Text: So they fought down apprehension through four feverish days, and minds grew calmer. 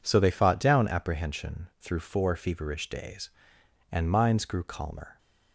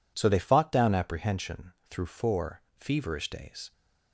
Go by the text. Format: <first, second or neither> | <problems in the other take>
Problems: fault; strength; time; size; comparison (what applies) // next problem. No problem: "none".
first | pauses between "apprehension" and "through"; slight; at 1.7 s; 0.18 s long // pauses between "four" and "feverish"; slight; at 2.6 s; 0.16 s long // stops before "and minds grew calmer"; at 3.7 s